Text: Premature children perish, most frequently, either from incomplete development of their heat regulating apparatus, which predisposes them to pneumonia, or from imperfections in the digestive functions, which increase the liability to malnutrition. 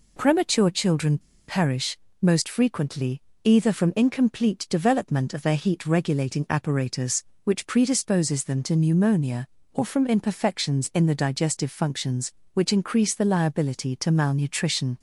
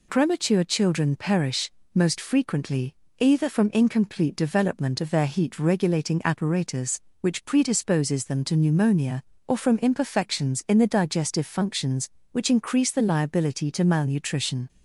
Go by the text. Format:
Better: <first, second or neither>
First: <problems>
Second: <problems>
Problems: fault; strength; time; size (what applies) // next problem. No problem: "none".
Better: second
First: pauses between "children" and "perish"; slight; at 1.1 s; 0.28 s long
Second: none